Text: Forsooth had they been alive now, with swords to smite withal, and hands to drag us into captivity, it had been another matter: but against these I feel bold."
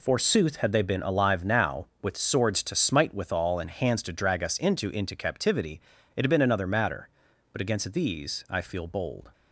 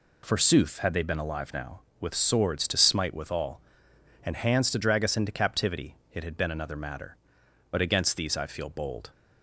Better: second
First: says "into" twice; at 4.8 s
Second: none

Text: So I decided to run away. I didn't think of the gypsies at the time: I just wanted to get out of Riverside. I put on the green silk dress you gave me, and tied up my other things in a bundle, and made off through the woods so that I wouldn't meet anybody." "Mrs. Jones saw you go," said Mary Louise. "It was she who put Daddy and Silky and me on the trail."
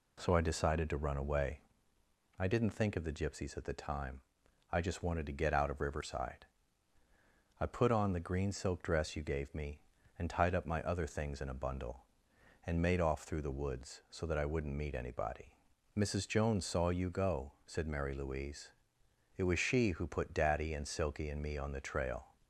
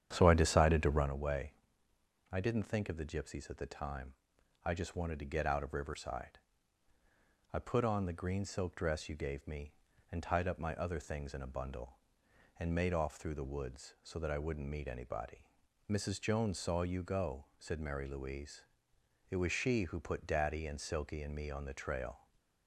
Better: first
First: none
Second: starts louder than the rest; strong; until 1.1 s; 9.5 dB

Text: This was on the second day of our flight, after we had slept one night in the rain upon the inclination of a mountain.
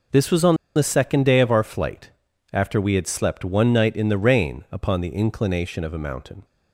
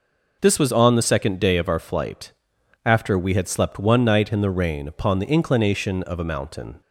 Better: second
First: pauses between "on" and "the"; slight; at 0.5 s; 0.20 s long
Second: none

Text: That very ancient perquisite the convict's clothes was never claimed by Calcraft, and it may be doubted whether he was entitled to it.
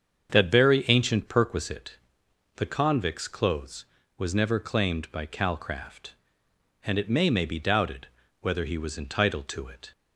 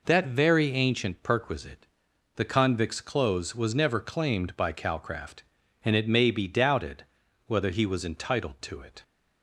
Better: second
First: starts louder than the rest; strong; until 1.3 s; 7.5 dB // pauses between "perquisite" and "the"; noticeable; at 1.9 s; 0.58 s long // says "may" twice; at 7.2 s // pauses between "doubted" and "whether"; slight; at 8.0 s; 0.32 s long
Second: pauses between "perquisite" and "the"; noticeable; at 1.8 s; 0.48 s long // pauses between "doubted" and "whether"; at 7.0 s; 0.42 s long

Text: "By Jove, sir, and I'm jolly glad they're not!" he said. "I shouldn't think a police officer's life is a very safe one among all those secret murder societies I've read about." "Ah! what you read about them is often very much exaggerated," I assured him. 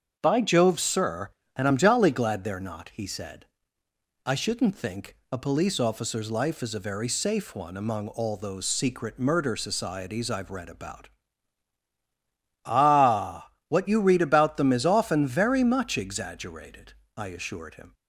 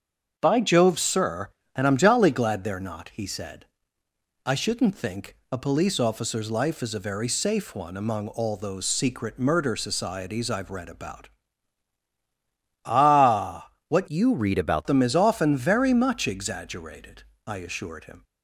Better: first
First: starts louder than the rest; until 1.2 s; 7 dB // pauses between "think" and "a"; slight; at 5.1 s; 0.16 s long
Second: starts louder than the rest; until 1.3 s; 7 dB // pauses between "think" and "a"; slight; at 5.3 s; 0.16 s long // changes voice from "you" to "about"; from 14.0 to 14.8 s; 0.8 s long

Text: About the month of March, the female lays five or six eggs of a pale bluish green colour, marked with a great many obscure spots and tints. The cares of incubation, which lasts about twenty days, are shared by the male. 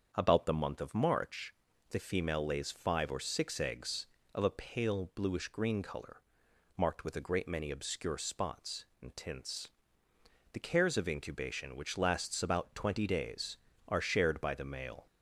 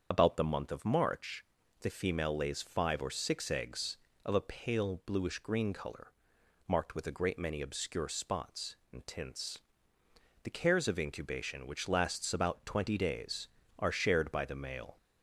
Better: first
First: starts louder than the rest; until 1.1 s; 7 dB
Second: loses the start of "About"; at 0.1 s; 55 ms // starts louder than the rest; until 1.1 s; 7 dB

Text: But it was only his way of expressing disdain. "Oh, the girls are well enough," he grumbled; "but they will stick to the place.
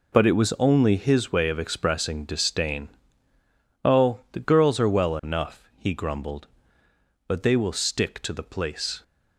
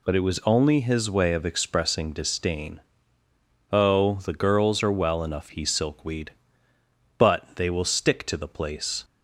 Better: first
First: none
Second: says "silkweed" for "grumbled"; at 5.6 s

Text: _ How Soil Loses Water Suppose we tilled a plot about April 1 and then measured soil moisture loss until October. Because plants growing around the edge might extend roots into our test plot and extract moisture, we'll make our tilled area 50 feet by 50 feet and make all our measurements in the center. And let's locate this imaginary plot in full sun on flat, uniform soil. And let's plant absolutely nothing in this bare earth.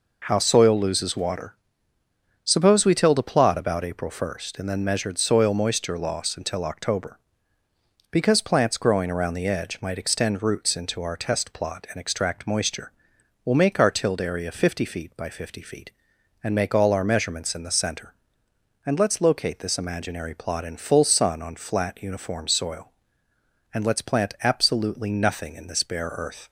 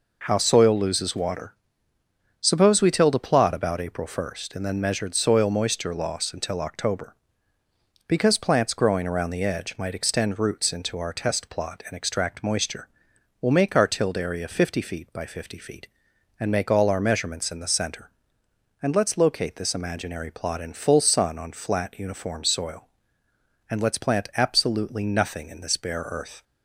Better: neither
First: pauses between "Water" and "Suppose"; noticeable; at 1.5 s; 0.90 s long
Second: pauses between "Water" and "Suppose"; noticeable; at 1.5 s; 0.88 s long

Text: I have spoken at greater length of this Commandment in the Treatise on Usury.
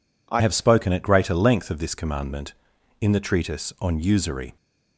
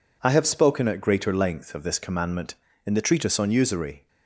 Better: second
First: changes voice at "have"; from 0.4 s on; 4.1 s long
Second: none

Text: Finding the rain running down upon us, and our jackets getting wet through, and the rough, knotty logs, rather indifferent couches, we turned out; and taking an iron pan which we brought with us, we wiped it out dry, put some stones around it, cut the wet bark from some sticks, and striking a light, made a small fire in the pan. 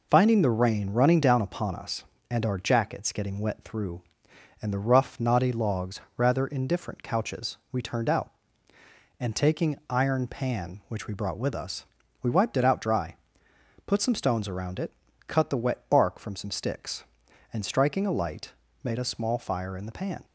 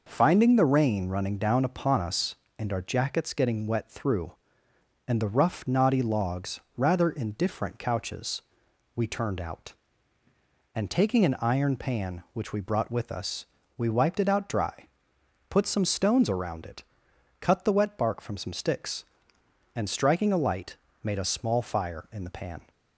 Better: second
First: skips "an"; at 9.8 s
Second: none

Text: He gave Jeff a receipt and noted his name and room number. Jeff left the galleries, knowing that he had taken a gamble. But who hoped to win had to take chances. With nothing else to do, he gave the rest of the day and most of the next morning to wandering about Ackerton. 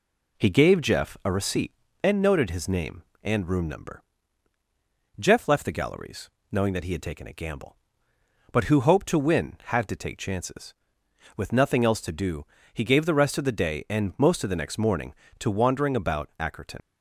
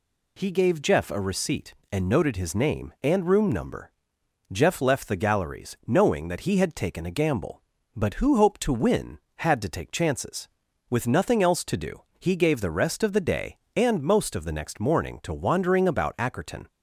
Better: second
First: leaves "Ackerton" unfinished; at 16.8 s; 70 ms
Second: none

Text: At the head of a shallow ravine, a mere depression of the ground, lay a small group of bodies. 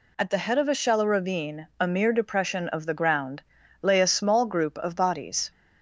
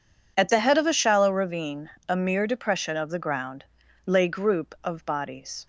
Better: first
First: none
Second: skips "a small"; at 4.2 s

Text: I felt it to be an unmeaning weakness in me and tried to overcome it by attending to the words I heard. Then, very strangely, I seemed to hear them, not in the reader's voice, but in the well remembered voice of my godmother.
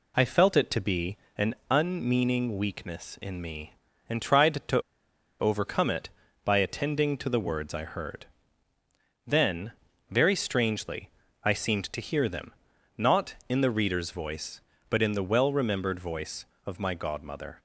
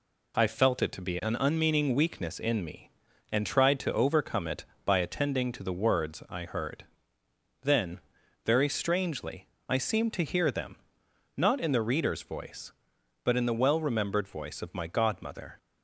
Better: second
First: pauses between "be" and "an"; slight; at 1.1 s; 0.20 s long // pauses between "to" and "overcome"; noticeable; at 4.7 s; 0.60 s long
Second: none

